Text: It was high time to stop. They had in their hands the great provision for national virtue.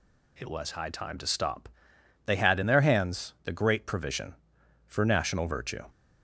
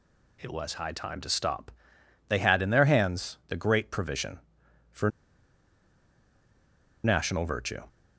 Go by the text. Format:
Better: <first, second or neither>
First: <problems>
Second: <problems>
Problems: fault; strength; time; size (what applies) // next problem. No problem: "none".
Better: first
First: none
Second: pauses between "for" and "national"; strong; at 5.0 s; 1.9 s long